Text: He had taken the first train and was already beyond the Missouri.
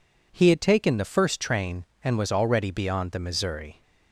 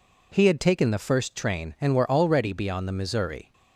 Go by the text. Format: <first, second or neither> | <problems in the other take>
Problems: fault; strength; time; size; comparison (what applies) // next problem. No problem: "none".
first | says "were" for "was"; at 1.9 s